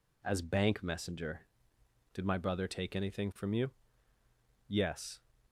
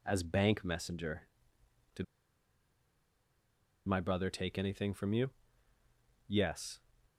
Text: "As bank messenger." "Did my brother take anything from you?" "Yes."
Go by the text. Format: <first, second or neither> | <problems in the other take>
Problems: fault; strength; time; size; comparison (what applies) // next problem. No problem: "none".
first | pauses between "Did" and "my"; strong; at 2.0 s; 1.8 s long